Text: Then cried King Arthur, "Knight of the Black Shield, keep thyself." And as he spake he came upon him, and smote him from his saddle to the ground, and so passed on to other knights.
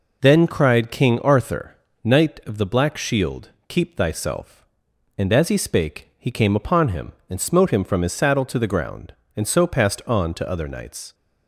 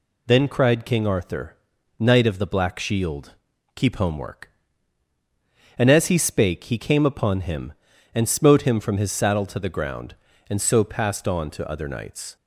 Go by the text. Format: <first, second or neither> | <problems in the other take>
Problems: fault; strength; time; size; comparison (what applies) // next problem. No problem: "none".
first | says "homework" for "thyself"; at 3.9 s